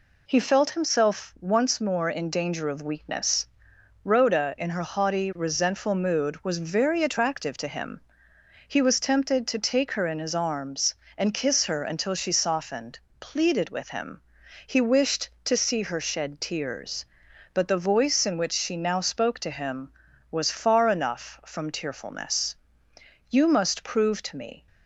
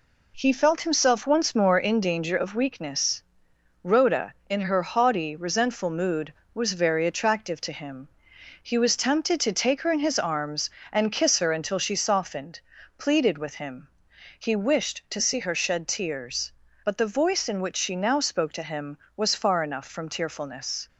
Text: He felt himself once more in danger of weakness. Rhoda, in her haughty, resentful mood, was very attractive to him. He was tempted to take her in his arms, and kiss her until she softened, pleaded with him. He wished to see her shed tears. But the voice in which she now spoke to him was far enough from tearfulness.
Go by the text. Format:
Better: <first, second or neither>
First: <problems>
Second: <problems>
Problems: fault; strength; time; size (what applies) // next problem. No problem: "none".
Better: second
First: goes on to say "You must prove to me"; from 23.3 s on; 1.3 s long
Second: none